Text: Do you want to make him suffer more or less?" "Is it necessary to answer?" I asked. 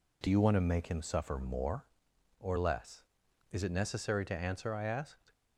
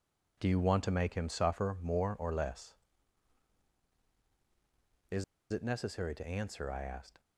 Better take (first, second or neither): first